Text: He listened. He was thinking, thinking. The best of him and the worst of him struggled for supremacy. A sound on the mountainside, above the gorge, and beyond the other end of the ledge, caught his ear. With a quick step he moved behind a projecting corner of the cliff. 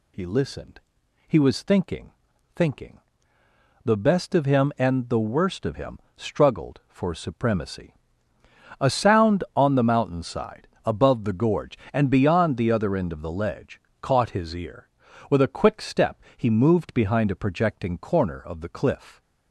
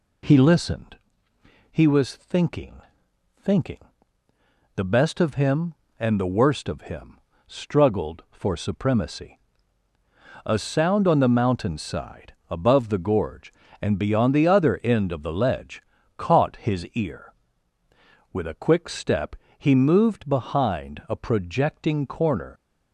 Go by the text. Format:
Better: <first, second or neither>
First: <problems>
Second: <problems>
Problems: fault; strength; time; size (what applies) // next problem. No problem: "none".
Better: first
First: pauses between "him" and "struggled"; slight; at 5.9 s; 0.16 s long // pauses between "step" and "he"; slight; at 16.2 s; 0.16 s long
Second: pauses between "him" and "struggled"; slight; at 7.1 s; 0.28 s long // pauses between "step" and "he"; slight; at 19.3 s; 0.22 s long // stops before "of the cliff"; at 22.5 s